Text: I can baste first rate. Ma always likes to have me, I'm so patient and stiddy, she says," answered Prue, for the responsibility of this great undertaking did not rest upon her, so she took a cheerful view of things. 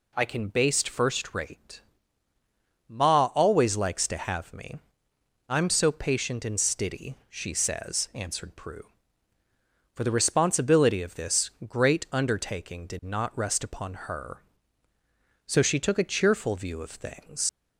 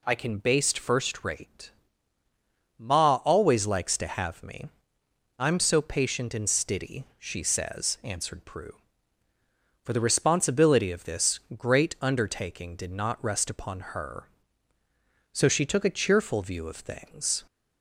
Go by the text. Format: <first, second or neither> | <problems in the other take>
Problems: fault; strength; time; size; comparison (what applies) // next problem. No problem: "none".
second | pauses between "this" and "great"; slight; at 11.4 s; 0.18 s long; slight in the second // leaves "things" unfinished; at 17.4 s; 120 ms